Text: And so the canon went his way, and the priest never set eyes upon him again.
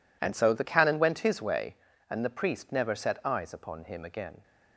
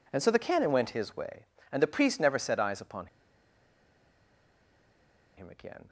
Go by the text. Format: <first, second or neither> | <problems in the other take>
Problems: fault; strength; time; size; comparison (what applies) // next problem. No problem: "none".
first | pauses between "upon" and "him"; strong; at 3.0 s; 2.2 s long